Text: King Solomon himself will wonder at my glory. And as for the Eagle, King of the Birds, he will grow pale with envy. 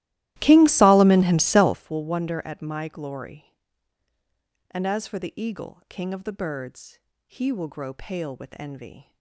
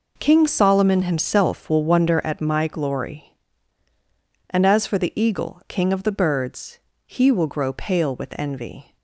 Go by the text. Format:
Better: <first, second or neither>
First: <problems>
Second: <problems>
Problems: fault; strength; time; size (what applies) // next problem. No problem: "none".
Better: second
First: starts louder than the rest; strong; until 1.9 s; 16 dB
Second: none